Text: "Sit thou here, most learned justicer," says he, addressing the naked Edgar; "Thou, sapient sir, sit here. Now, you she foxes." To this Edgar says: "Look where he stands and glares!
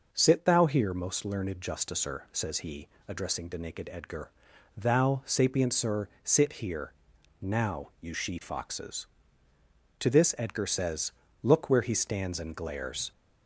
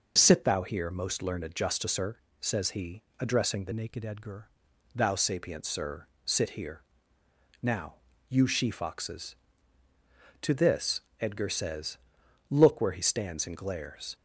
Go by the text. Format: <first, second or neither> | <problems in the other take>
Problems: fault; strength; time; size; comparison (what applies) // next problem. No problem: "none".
first | changes voice from "naked" to "Edgar"; from 3.7 to 4.4 s; 0.7 s long // pauses between "this" and "Edgar"; slight; at 11.0 s; 0.18 s long